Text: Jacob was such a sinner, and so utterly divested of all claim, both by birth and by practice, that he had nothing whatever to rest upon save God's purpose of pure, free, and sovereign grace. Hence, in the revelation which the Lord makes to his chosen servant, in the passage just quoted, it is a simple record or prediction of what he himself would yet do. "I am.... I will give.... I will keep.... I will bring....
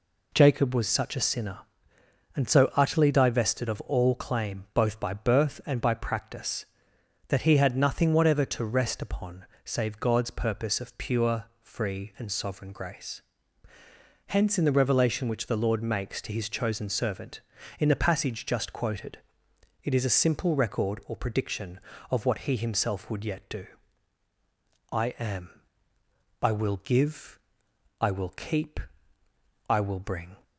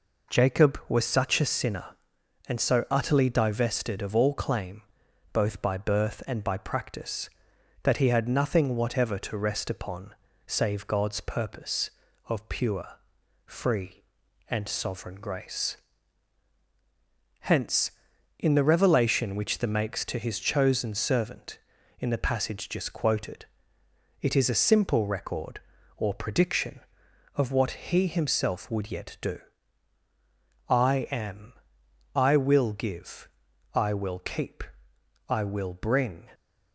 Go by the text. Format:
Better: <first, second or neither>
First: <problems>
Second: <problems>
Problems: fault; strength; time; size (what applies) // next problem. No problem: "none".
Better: first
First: pauses between "upon" and "save"; slight; at 9.4 s; 0.18 s long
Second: pauses between "upon" and "save"; slight; at 10.1 s; 0.32 s long // skips "Lord"; at 19.6 s